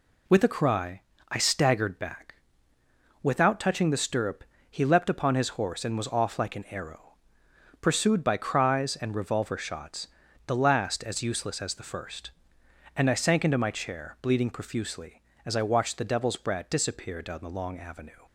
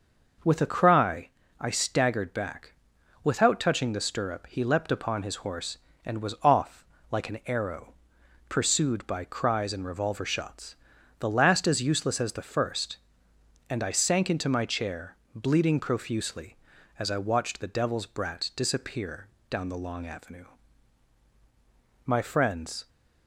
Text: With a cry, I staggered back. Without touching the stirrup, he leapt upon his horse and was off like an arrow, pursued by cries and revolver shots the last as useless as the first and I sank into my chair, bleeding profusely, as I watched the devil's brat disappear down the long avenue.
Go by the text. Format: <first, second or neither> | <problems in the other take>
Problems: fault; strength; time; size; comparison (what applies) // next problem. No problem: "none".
first | pauses between "off" and "like"; slight; at 6.8 s; 0.26 s long // pauses between "shots" and "the"; noticeable; at 10.7 s; 0.46 s long; also in the first // pauses between "disappear" and "down"; slight; at 19.2 s; 0.22 s long // goes on to say "My friends"; noticeable; from 22.0 s on; 0.82 s long